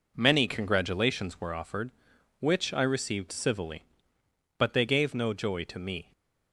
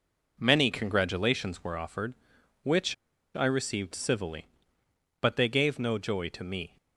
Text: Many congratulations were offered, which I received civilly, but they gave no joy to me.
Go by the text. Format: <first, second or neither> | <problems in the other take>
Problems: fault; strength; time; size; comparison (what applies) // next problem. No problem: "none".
first | pauses between "which" and "I"; at 2.9 s; 0.39 s long